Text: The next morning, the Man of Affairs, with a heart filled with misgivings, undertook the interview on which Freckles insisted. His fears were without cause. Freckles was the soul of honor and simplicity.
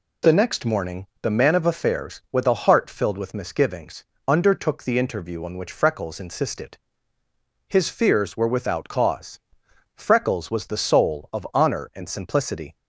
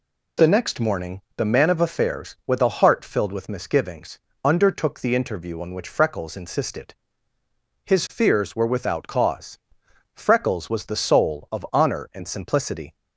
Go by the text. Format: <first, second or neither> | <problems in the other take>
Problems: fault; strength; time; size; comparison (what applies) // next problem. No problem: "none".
neither | none